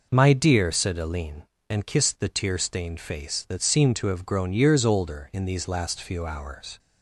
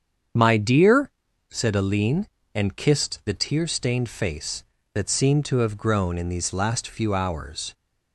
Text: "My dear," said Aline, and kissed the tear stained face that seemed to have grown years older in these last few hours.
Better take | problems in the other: first | starts louder than the rest; strong; until 1.7 s; 7.5 dB // skips "years older"; at 6.1 s

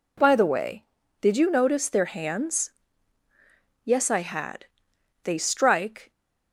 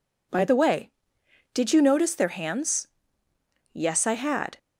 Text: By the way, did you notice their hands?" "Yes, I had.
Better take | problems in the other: second | goes on to say "They strike"; noticeable; from 5.2 s on; 0.88 s long

